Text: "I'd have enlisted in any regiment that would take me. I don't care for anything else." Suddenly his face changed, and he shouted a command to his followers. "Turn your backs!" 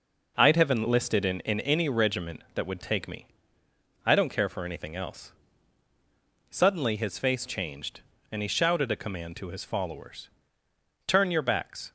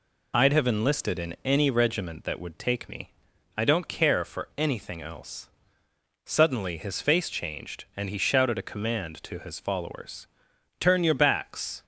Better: second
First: says "in" twice; at 1.4 s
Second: none

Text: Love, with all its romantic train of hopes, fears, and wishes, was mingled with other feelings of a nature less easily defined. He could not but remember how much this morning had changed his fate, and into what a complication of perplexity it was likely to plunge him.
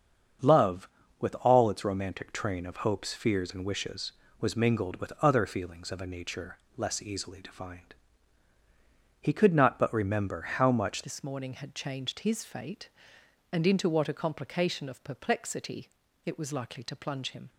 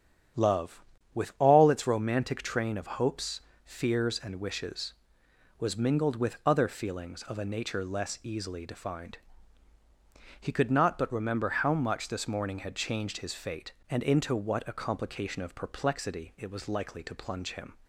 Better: second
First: starts louder than the rest; strong; until 1.8 s; 7.5 dB // pauses between "nature" and "less"; slight; at 6.5 s; 0.18 s long // changes voice at "this"; from 11.0 s on; 6.4 s long // pauses between "perplexity" and "it"; slight; at 15.8 s; 0.36 s long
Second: starts louder than the rest; strong; until 1.7 s; 9 dB

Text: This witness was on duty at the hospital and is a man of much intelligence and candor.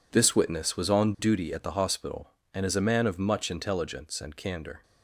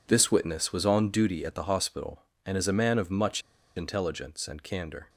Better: first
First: none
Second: pauses between "much" and "intelligence"; slight; at 3.4 s; 0.35 s long

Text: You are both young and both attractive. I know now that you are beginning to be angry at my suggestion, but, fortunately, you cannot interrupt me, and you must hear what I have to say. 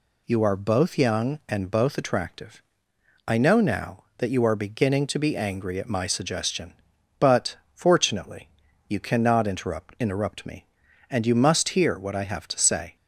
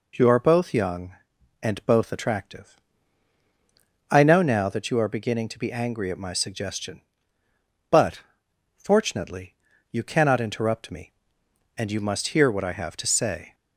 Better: second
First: says "interrupt" twice; at 9.9 s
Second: none

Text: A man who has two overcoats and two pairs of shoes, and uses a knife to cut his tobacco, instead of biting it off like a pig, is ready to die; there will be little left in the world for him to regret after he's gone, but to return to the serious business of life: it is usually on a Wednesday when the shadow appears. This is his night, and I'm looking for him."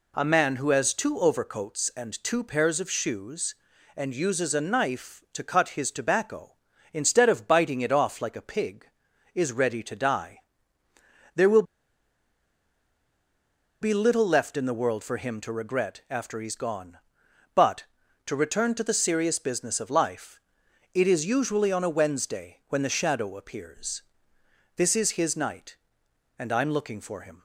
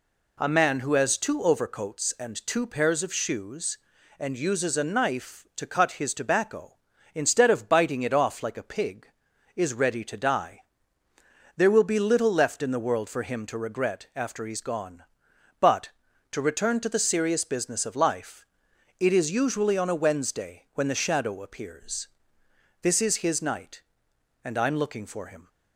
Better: second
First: pauses between "will" and "be"; strong; at 11.6 s; 2.1 s long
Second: none

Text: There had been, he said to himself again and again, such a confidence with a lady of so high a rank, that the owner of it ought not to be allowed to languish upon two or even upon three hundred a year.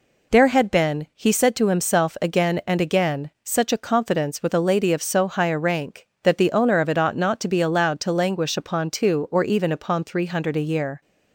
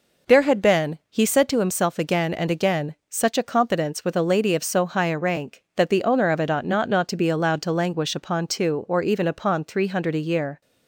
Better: first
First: none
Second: says "not" twice; at 6.8 s

